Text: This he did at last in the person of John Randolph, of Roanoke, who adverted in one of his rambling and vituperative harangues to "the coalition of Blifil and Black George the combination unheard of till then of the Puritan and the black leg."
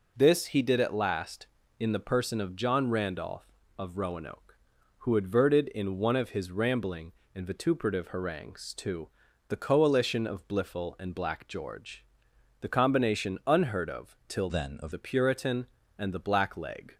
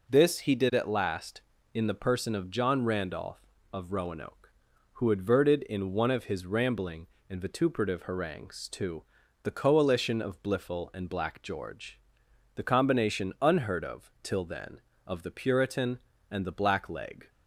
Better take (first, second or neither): second